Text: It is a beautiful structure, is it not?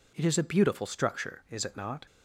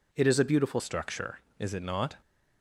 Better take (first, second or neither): first